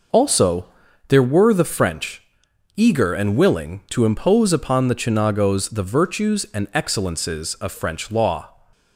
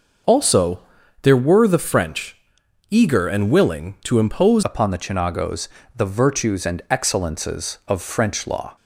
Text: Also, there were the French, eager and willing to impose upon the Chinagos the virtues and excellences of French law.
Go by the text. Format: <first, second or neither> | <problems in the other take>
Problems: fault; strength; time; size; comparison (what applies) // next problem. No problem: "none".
first | changes voice at "upon"; from 4.6 s on; 4.1 s long // pauses between "Chinagos" and "the"; slight; at 5.6 s; 0.28 s long